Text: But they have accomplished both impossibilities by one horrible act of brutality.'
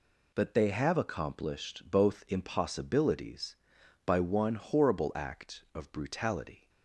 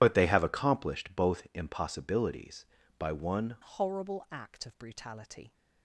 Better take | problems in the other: first | changes voice at "horrible"; from 3.6 s on; 1.9 s long

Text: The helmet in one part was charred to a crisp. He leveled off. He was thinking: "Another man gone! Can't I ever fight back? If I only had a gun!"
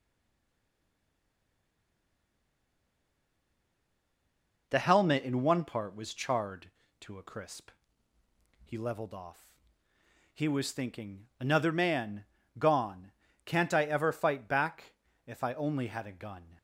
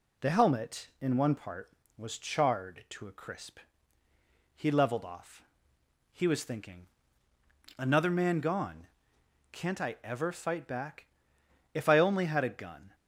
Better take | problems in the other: second | stays silent before the first word; strong; until 4.6 s; 4.6 s long // pauses between "man" and "gone"; slight; at 12.2 s; 0.34 s long

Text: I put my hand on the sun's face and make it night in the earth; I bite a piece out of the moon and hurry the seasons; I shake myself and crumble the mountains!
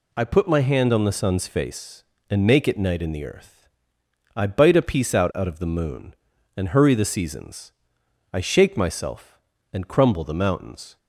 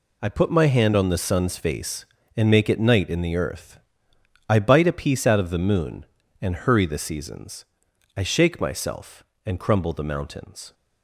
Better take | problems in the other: second | says "out" twice; at 5.3 s

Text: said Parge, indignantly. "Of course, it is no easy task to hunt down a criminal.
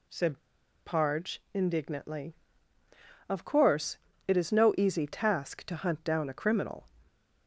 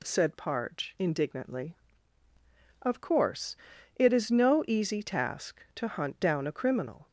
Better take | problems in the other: second | pauses between "said" and "Parge"; noticeable; at 0.3 s; 0.48 s long

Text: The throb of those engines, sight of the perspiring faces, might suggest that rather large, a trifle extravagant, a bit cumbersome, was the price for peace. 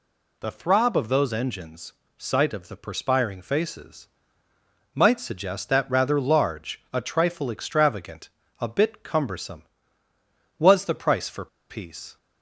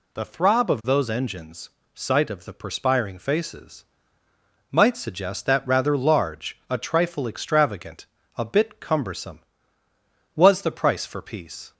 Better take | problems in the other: second | pauses between "for" and "peace"; slight; at 11.4 s; 0.23 s long

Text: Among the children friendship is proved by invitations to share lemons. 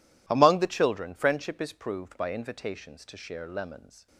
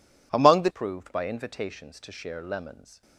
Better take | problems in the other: first | skips "children friendship is"; at 0.6 s

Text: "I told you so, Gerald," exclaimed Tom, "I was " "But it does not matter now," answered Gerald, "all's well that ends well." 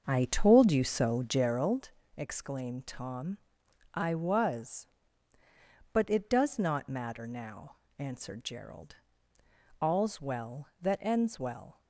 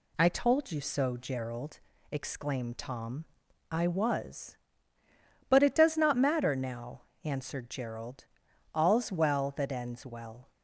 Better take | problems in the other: second | starts louder than the rest; until 1.8 s; 7 dB

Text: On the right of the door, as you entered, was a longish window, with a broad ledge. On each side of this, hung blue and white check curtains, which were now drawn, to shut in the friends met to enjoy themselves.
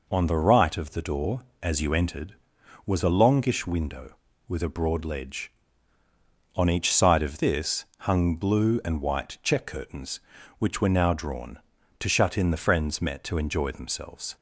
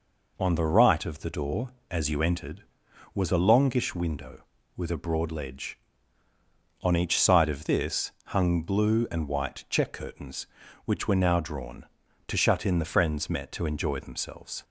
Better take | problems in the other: neither | none

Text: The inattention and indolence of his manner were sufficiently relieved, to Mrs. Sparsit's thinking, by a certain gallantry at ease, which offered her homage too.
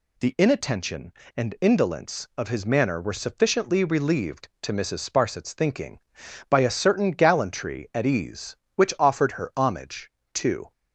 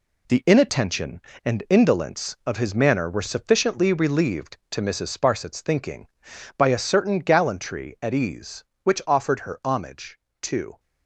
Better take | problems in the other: first | gets quieter; strong; throughout; 8 dB // pauses between "homage" and "too"; slight; at 10.1 s; 0.22 s long; slight in the first

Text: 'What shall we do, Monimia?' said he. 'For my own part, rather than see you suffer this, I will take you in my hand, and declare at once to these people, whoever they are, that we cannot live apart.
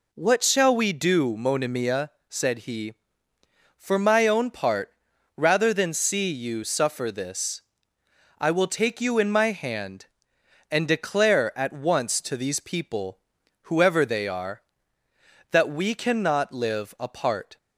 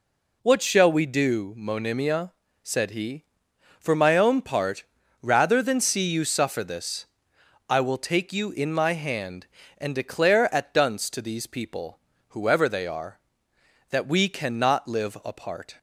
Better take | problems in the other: first | says "dunce" for "once"; at 10.7 s

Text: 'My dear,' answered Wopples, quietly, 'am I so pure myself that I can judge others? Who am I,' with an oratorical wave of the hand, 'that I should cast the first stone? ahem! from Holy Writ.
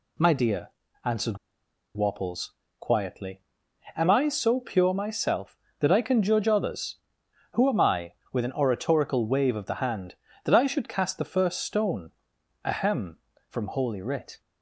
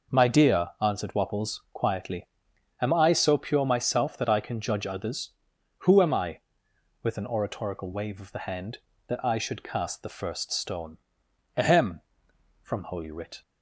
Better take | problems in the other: second | pauses between "answered" and "Wopples"; noticeable; at 1.3 s; 0.58 s long

